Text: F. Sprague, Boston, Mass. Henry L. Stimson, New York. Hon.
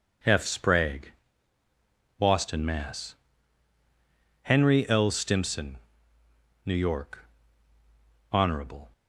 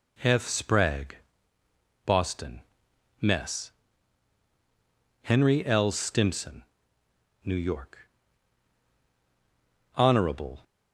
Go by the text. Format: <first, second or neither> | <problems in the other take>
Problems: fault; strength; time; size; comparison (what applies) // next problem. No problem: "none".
first | says "Mess" for "Mass"; at 3.2 s